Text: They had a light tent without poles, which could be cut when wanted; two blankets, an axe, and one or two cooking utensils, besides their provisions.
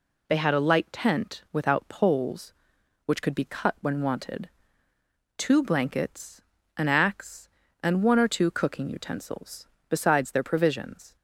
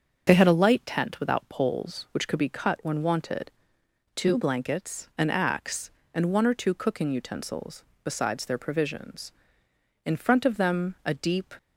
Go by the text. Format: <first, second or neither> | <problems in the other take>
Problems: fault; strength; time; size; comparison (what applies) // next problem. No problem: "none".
first | starts louder than the rest; until 1.2 s; 7 dB // goes on to say "In front of them a deep"; from 10.0 s on; 1.5 s long